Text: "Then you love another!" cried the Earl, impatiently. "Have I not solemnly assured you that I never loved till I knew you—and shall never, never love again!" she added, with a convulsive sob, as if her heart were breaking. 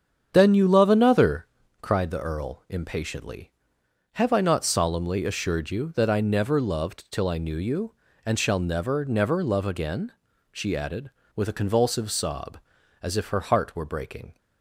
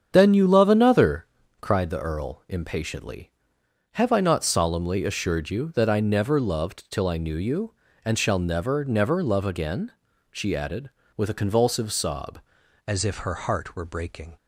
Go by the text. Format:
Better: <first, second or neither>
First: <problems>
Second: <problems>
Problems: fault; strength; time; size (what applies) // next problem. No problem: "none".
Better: first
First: starts louder than the rest; strong; until 1.3 s; 8 dB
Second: starts louder than the rest; strong; until 1.1 s; 8 dB // changes voice at "as"; from 12.8 s on; 1.5 s long